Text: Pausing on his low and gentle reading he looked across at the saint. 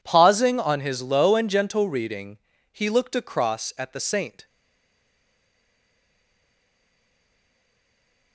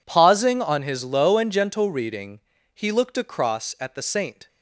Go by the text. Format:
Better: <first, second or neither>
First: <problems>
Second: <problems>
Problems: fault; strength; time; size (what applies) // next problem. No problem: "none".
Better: second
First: pauses between "reading" and "he"; slight; at 2.3 s; 0.36 s long // stays silent after the last word; strong; from 4.4 s on; 3.9 s long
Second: pauses between "reading" and "he"; slight; at 2.3 s; 0.36 s long